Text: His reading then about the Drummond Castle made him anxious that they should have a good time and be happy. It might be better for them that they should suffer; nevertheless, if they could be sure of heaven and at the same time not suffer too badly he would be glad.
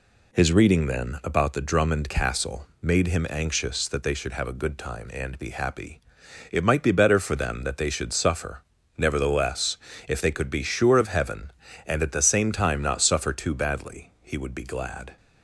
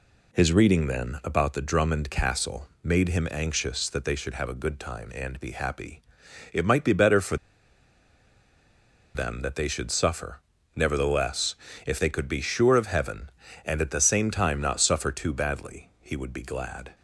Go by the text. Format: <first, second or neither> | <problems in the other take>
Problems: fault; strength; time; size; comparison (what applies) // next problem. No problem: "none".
first | pauses between "Castle" and "made"; slight; at 2.6 s; 0.16 s long; slight in the first // pauses between "for" and "them"; strong; at 7.3 s; 1.7 s long